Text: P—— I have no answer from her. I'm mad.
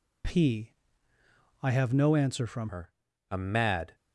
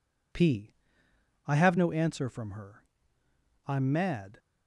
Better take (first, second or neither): second